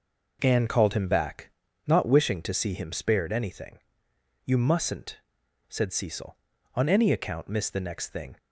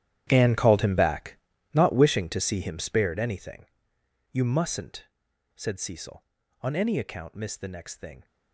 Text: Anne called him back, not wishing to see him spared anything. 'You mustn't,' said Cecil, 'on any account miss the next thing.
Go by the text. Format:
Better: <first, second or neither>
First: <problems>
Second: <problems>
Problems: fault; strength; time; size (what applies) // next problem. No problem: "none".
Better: first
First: none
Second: gets quieter; strong; throughout; 16 dB